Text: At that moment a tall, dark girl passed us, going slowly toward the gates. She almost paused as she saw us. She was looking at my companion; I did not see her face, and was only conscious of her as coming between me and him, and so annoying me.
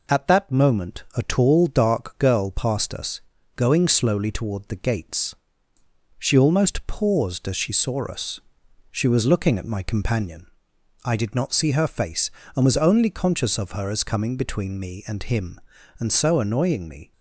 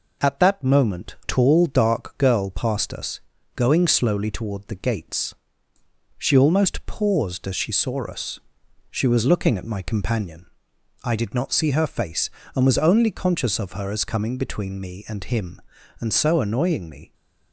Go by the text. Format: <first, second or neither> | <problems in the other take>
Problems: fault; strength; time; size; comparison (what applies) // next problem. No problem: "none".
first | skips "a"; at 1.1 s